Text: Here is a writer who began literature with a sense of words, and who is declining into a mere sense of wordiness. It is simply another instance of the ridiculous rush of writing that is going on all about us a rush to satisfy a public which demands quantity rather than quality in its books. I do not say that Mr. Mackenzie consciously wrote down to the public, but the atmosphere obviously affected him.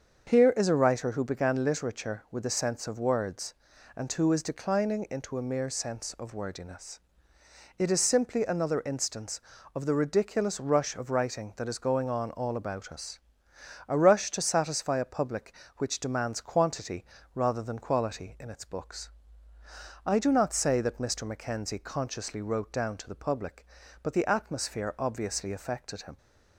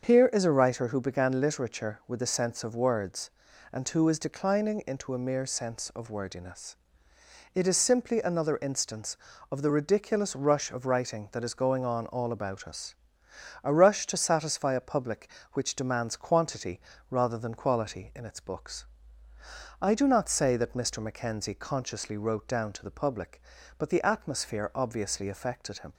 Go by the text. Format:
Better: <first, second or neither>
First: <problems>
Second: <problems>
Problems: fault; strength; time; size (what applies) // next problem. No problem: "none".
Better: neither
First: starts louder than the rest; until 1.3 s; 7 dB // pauses between "us" and "a"; noticeable; at 13.1 s; 0.68 s long // pauses between "quantity" and "rather"; slight; at 17.0 s; 0.28 s long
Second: starts louder than the rest; until 1.1 s; 7 dB // pauses between "us" and "a"; noticeable; at 12.9 s; 0.68 s long // pauses between "quantity" and "rather"; slight; at 16.8 s; 0.28 s long